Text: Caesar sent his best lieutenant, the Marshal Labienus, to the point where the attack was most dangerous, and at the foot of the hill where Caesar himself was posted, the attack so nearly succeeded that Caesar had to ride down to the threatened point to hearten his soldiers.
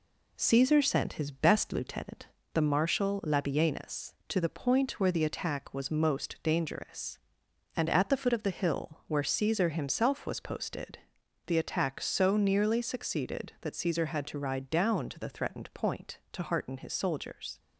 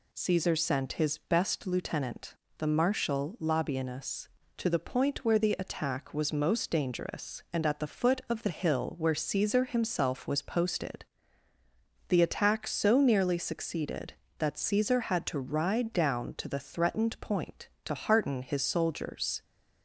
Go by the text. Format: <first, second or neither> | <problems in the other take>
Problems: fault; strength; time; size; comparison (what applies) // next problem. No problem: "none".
second | gets quieter; throughout; 3.5 dB